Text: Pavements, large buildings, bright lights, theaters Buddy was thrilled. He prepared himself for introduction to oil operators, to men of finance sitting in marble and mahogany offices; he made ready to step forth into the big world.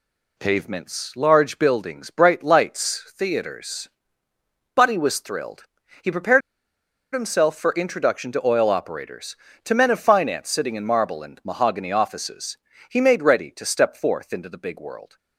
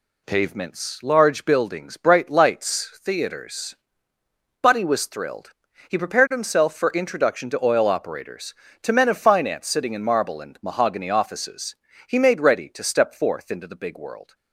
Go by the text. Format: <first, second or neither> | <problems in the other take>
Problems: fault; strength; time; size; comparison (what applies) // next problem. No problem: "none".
second | pauses between "theaters" and "Buddy"; noticeable; at 3.8 s; 0.86 s long; noticeable in the second // pauses between "prepared" and "himself"; noticeable; at 6.4 s; 0.74 s long